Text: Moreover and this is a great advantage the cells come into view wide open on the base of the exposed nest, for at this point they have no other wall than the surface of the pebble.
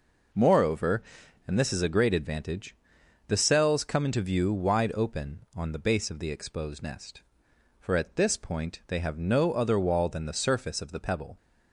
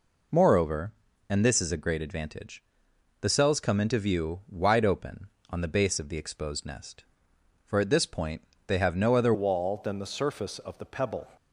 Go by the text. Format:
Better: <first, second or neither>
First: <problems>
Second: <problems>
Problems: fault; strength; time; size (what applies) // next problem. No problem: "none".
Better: first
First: pauses between "advantage" and "the"; noticeable; at 2.7 s; 0.52 s long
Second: pauses between "advantage" and "the"; noticeable; at 2.6 s; 0.58 s long // pauses between "point" and "they"; slight; at 8.4 s; 0.24 s long // changes voice at "wall"; from 9.3 s on; 1.9 s long